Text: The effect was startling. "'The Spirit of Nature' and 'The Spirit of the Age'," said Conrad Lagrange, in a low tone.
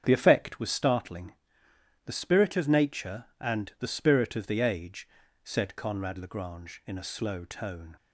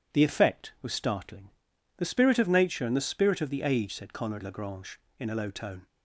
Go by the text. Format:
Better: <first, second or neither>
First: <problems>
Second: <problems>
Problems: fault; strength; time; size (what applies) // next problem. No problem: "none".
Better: second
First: starts louder than the rest; strong; until 1.0 s; 8 dB // says "slow" for "low"; at 7.0 s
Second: none